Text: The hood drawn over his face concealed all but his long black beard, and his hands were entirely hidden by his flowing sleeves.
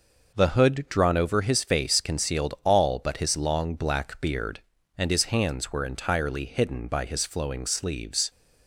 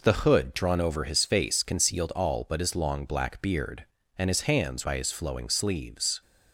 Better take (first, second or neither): first